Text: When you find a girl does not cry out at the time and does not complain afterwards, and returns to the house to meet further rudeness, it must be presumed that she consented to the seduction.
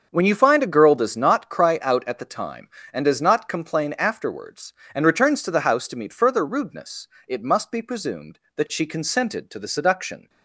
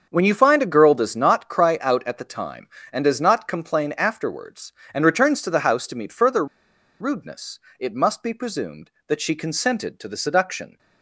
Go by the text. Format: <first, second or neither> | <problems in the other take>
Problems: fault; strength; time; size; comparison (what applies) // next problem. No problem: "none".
first | starts louder than the rest; until 1.1 s; 7 dB; also in the first // pauses between "further" and "rudeness"; noticeable; at 6.4 s; 0.54 s long